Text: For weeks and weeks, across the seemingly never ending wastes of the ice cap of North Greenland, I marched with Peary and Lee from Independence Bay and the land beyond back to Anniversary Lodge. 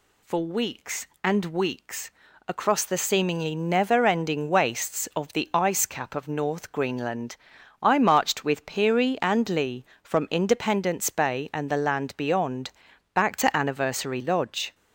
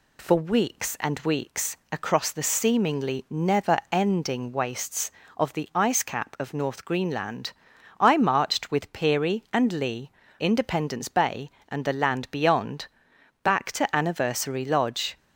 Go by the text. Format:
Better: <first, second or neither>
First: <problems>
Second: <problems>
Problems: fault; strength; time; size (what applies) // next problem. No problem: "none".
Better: first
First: pauses between "beyond" and "back"; at 12.7 s; 0.44 s long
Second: skips "from"; at 10.2 s // pauses between "beyond" and "back"; noticeable; at 12.8 s; 0.54 s long